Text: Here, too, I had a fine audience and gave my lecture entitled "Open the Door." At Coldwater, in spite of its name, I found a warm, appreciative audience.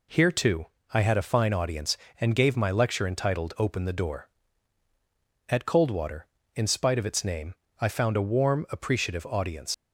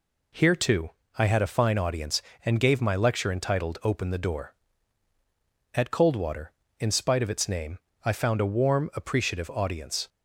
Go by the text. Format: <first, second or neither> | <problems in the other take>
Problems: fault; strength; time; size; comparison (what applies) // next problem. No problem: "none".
second | leaves "audience" unfinished; at 9.7 s; 95 ms